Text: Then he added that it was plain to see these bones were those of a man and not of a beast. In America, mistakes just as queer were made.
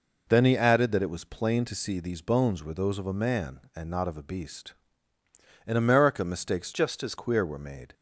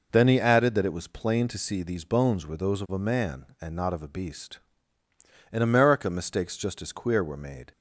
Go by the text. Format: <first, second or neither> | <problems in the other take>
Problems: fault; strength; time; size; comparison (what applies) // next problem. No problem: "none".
second | changes voice from "just" to "as"; from 6.7 to 7.1 s; 0.4 s long